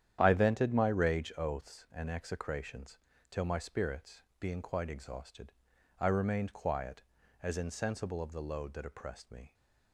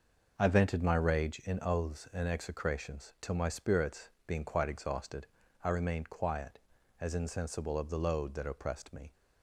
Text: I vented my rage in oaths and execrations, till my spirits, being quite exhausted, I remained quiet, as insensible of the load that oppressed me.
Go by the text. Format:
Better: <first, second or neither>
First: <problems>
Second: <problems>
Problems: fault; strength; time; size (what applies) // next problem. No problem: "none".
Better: second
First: starts louder than the rest; strong; until 1.2 s; 10 dB // skips "in"; at 1.3 s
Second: none